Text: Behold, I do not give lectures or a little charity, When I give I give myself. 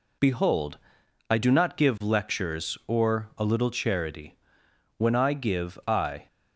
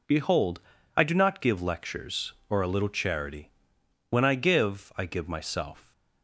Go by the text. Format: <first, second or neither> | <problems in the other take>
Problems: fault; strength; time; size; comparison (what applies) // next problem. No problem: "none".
second | stops before "give myself"; at 6.2 s